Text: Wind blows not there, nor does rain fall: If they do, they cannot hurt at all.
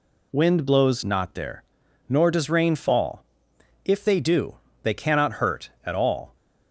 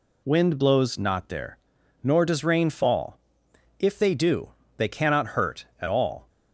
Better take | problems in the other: neither | none

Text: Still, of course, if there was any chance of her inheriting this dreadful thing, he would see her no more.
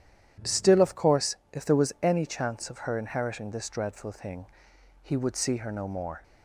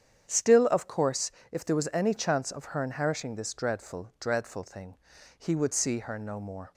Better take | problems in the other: first | starts louder than the rest; strong; until 1.3 s; 8.5 dB // says "dreadful" twice; at 4.1 s

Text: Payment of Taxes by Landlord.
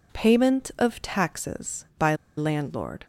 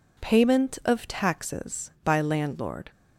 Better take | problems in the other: second | pauses between "by" and "Landlord"; slight; at 2.1 s; 0.20 s long

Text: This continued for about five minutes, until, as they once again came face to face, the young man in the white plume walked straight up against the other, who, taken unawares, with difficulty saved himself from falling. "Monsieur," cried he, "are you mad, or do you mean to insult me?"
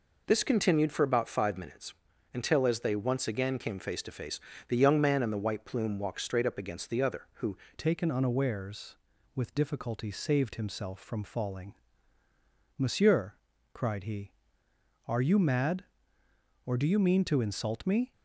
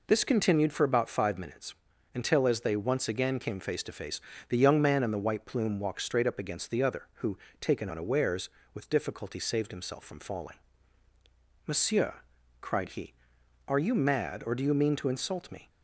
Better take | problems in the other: second | changes voice at "taken"; from 7.7 s on; 10.4 s long

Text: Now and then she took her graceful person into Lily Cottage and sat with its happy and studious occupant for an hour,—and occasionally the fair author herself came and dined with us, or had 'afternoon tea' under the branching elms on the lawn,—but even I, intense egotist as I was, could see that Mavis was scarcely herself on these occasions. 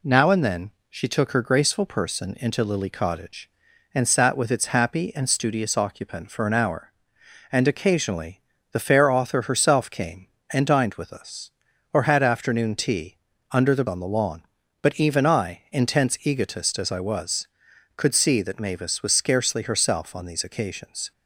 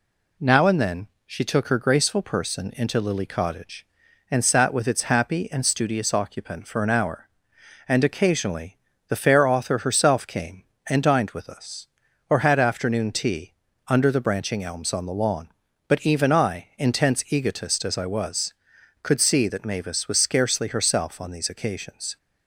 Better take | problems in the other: second | pauses between "then" and "she"; slight; at 0.7 s; 0.18 s long; slight in the second // pauses between "occasionally" and "the"; slight; at 8.4 s; 0.30 s long; slight in the second // pauses between "tea" and "under"; slight; at 13.1 s; 0.34 s long; slight in the second // skips "branching elms"; at 13.8 s

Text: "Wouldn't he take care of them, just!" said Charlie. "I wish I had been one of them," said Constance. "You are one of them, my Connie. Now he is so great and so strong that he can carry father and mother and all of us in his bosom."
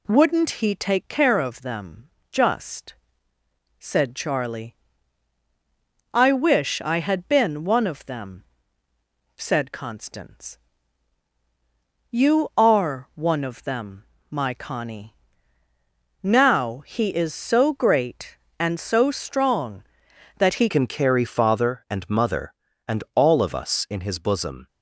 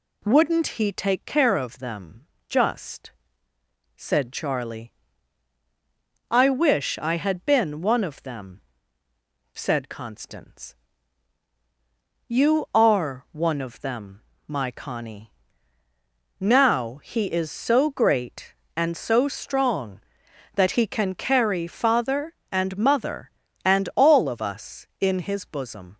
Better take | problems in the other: second | changes voice at "can"; from 20.7 s on; 3.9 s long

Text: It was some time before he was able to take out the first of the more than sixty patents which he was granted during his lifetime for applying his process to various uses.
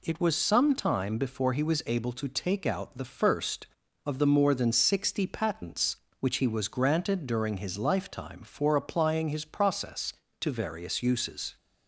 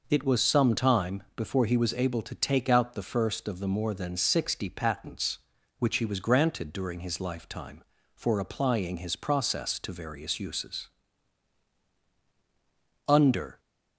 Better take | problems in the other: first | goes on to say "Under"; from 13.0 s on; 0.52 s long

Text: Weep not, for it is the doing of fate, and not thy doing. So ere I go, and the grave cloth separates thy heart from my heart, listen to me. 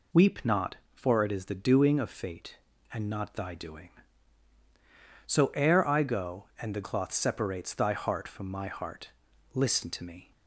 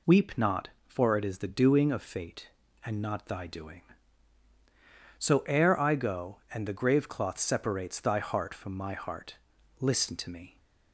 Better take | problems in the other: second | skips "grave"; at 6.8 s

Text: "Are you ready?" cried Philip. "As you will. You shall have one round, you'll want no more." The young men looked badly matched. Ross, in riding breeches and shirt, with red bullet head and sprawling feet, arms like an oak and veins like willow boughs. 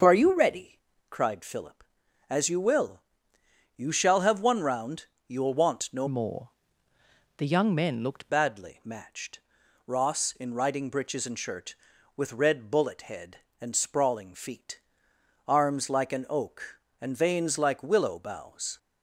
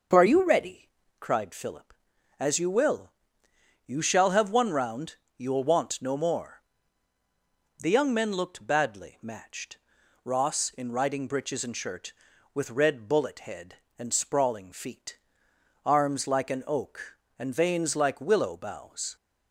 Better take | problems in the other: second | starts louder than the rest; until 1.3 s; 6.5 dB; also in the second // changes voice from "more" to "looked"; from 6.0 to 8.2 s; 2.2 s long

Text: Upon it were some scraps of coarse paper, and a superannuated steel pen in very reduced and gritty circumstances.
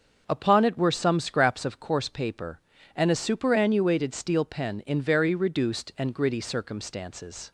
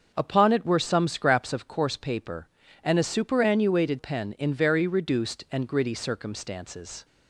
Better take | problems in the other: first | starts louder than the rest; until 1.1 s; 6.5 dB; also in the first // skips "steel"; at 3.9 s

